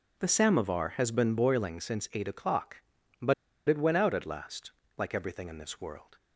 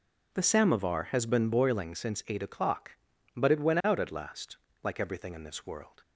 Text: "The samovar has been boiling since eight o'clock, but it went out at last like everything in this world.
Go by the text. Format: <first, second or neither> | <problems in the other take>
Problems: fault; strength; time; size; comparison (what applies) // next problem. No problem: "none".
second | pauses between "but" and "it"; slight; at 3.3 s; 0.33 s long // pauses between "last" and "like"; slight; at 4.7 s; 0.24 s long; slight in the second